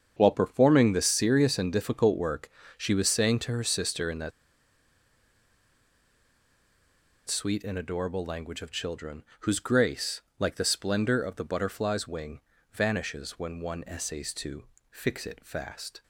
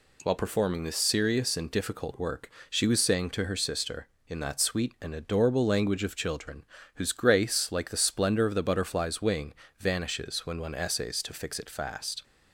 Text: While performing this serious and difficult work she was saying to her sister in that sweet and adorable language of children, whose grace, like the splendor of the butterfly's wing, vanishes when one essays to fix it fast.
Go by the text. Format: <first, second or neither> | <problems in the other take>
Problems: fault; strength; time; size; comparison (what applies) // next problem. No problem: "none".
second | starts louder than the rest; strong; until 1.1 s; 7.5 dB // pauses between "work" and "she"; slight; at 2.4 s; 0.26 s long; slight in the second // pauses between "that" and "sweet"; strong; at 4.3 s; 2.9 s long // pauses between "to" and "fix"; slight; at 14.6 s; 0.26 s long